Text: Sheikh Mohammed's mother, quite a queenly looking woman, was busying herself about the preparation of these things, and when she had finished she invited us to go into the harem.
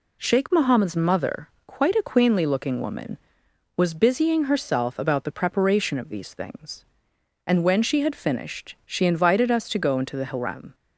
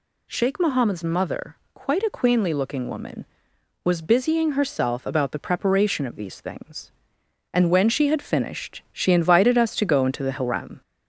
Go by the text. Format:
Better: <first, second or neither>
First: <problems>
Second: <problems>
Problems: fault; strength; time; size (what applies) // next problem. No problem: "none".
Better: first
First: none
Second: gets louder; slight; throughout; 2.5 dB